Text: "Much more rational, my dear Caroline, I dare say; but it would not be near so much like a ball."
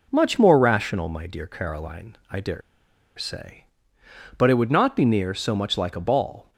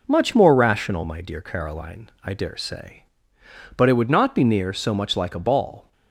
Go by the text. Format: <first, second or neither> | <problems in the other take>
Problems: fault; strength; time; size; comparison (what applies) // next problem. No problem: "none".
second | pauses between "dare" and "say"; noticeable; at 2.6 s; 0.57 s long